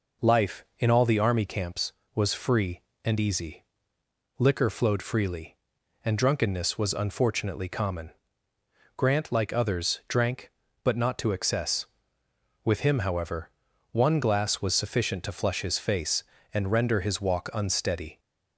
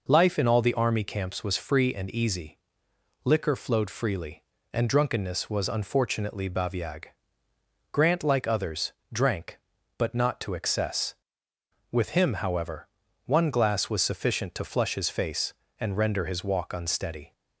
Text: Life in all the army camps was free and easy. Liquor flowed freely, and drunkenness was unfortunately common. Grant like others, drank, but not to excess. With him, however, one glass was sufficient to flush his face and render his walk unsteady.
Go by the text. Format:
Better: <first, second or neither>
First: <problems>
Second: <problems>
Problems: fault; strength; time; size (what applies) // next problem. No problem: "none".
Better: first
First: none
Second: says "baviag" for "common"; at 6.4 s